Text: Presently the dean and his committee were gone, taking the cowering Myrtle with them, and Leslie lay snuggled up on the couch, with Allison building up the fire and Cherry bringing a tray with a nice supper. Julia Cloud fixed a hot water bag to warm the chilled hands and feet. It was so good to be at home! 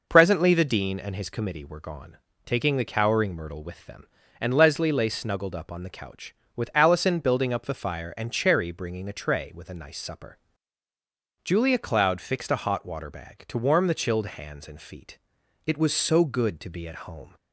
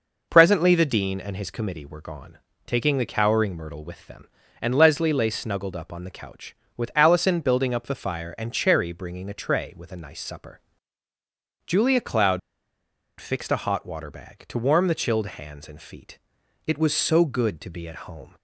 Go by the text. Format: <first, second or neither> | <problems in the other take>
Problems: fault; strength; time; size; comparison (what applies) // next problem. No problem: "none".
first | pauses between "Cloud" and "fixed"; noticeable; at 12.3 s; 0.80 s long